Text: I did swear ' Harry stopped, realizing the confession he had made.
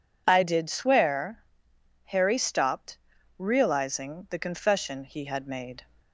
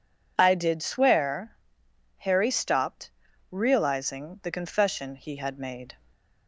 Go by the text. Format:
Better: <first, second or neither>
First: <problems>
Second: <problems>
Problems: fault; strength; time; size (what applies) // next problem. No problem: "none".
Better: neither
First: none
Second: none